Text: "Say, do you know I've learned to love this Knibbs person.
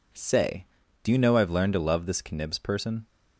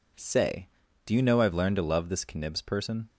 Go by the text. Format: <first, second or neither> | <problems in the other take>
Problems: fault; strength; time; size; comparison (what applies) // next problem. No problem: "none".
neither | none